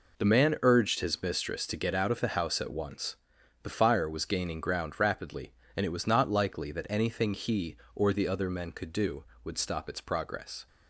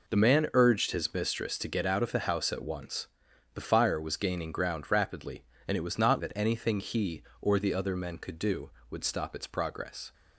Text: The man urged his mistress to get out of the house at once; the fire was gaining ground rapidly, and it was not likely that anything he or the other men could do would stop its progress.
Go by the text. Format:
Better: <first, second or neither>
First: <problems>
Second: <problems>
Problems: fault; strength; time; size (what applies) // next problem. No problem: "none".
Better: first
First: none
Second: skips "likely"; at 6.1 s